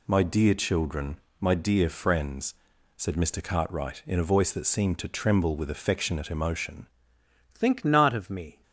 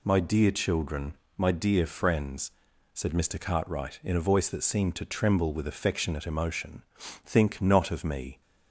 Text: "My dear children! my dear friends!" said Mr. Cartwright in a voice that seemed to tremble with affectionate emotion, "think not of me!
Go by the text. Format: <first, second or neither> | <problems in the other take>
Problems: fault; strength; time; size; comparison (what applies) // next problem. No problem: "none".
second | changes voice at "think"; from 7.5 s on; 1.1 s long